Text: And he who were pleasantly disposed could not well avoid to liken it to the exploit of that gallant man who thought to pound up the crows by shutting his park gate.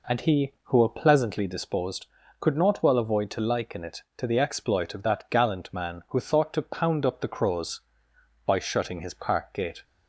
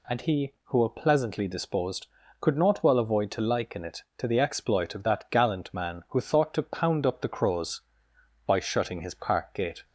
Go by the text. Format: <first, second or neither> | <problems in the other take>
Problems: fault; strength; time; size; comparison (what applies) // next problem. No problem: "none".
second | starts louder than the rest; until 1.5 s; 4 dB